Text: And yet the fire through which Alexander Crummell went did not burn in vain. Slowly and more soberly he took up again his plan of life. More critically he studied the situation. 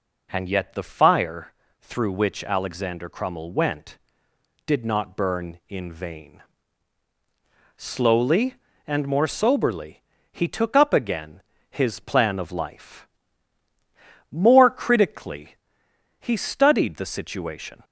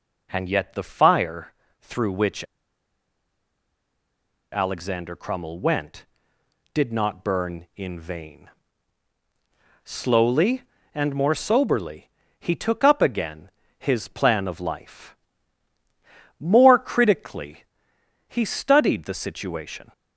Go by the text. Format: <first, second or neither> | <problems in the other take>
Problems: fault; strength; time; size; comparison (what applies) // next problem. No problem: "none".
first | pauses between "fire" and "through"; slight; at 1.5 s; 0.30 s long; slight in the first // pauses between "which" and "Alexander"; strong; at 2.4 s; 2.0 s long // pauses between "soberly" and "he"; slight; at 12.1 s; 0.28 s long; slight in the first // pauses between "again" and "his"; slight; at 13.5 s; 0.28 s long; slight in the first // pauses between "critically" and "he"; noticeable; at 17.6 s; 0.64 s long; noticeable in the first